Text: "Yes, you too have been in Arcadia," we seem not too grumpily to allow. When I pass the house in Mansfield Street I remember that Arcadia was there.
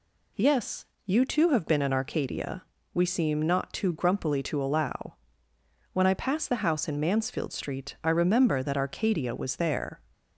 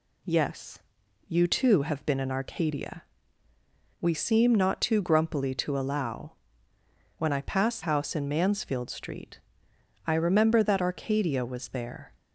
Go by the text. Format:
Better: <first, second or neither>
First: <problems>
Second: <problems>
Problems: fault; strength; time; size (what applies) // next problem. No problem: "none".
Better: first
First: none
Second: skips "the"; at 7.8 s // pauses between "Street" and "I"; noticeable; at 9.4 s; 0.66 s long